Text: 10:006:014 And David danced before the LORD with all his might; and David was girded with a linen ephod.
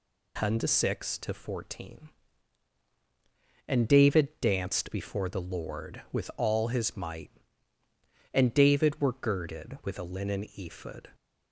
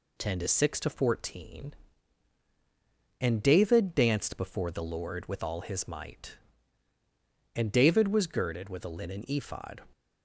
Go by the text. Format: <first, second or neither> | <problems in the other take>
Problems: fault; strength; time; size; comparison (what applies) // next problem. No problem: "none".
second | says "were" for "was"; at 9.0 s